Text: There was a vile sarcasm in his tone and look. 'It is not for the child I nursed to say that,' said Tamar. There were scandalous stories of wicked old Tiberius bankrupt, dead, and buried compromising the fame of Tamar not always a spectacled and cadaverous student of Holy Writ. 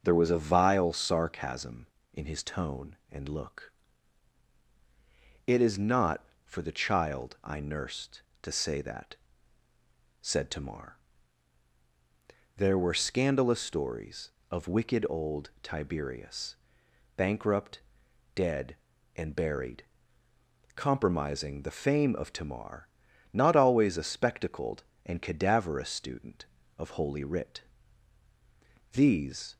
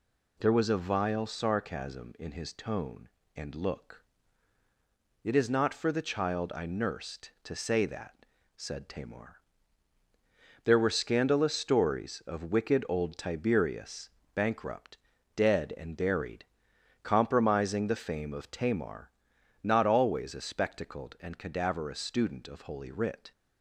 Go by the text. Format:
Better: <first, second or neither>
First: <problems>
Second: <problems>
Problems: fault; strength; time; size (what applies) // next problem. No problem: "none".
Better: second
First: starts louder than the rest; noticeable; until 1.0 s; 6 dB // pauses between "Tiberius" and "bankrupt"; noticeable; at 16.5 s; 0.62 s long // pauses between "buried" and "compromising"; noticeable; at 19.8 s; 0.94 s long // pauses between "Tamar" and "not"; noticeable; at 22.8 s; 0.46 s long // goes on to say "These"; noticeable; from 28.9 s on; 0.64 s long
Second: pauses between "Tiberius" and "bankrupt"; slight; at 14.0 s; 0.26 s long // pauses between "buried" and "compromising"; noticeable; at 16.4 s; 0.56 s long // pauses between "Tamar" and "not"; noticeable; at 19.0 s; 0.54 s long